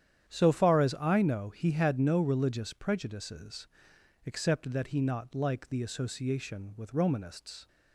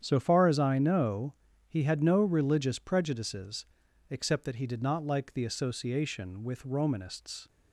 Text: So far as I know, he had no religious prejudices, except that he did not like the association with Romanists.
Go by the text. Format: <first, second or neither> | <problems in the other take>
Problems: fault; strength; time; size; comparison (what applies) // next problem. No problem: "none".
second | starts louder than the rest; strong; until 1.3 s; 10 dB; strong in the second // skips "did"; at 5.0 s